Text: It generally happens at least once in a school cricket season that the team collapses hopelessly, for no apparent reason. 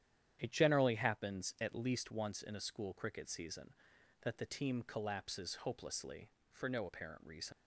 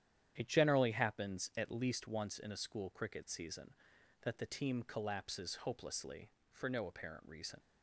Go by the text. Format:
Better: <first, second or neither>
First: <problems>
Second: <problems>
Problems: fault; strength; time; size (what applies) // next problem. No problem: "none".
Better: second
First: starts louder than the rest; strong; until 1.4 s; 10 dB // leaves "reason" unfinished; at 7.5 s; 45 ms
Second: starts louder than the rest; strong; until 1.3 s; 10 dB